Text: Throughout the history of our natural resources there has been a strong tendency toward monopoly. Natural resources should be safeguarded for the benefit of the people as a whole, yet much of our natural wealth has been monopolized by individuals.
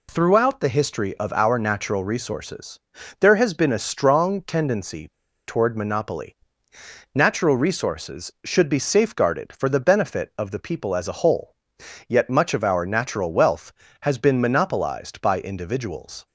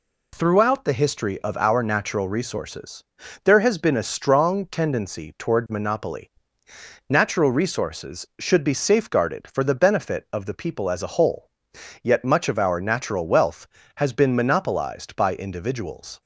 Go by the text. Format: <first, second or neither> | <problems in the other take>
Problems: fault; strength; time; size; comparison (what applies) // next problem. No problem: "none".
second | pauses between "resources" and "there"; at 2.7 s; 0.40 s long; also in the second // pauses between "tendency" and "toward"; at 5.0 s; 0.38 s long